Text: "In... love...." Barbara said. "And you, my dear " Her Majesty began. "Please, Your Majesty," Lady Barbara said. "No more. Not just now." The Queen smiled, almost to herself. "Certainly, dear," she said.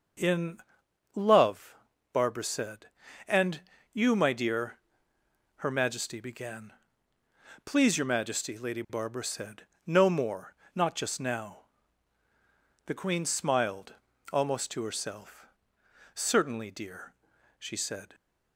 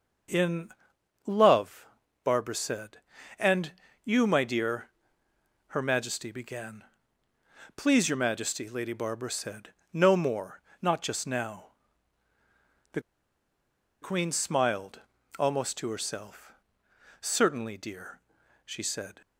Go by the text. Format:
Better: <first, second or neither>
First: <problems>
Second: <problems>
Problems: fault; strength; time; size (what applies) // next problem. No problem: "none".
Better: first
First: starts louder than the rest; until 1.7 s; 6.5 dB // pauses between "And" and "you"; slight; at 3.6 s; 0.30 s long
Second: starts louder than the rest; until 1.8 s; 6.5 dB // pauses between "And" and "you"; slight; at 3.7 s; 0.30 s long // pauses between "The" and "Queen"; at 13.0 s; 1.0 s long